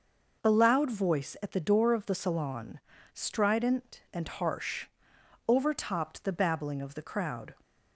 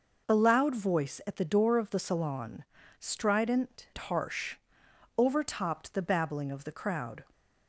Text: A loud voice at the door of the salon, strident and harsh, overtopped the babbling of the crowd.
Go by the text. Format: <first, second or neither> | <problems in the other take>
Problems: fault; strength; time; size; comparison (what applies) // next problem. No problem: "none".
first | skips "and"; at 3.9 s